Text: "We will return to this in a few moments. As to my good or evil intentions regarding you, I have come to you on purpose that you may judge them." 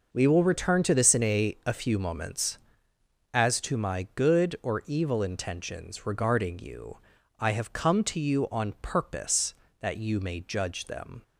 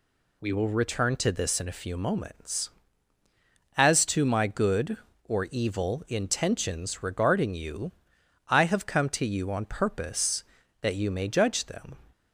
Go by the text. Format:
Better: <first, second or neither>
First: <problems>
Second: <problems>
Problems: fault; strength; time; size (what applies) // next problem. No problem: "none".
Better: second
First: says "a" twice; at 1.6 s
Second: none